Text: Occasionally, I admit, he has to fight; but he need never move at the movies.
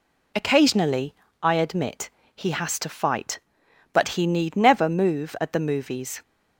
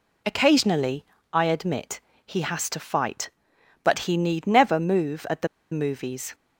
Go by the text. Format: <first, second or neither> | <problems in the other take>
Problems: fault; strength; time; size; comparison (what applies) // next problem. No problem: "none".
first | pauses between "the" and "movies"; slight; at 5.4 s; 0.24 s long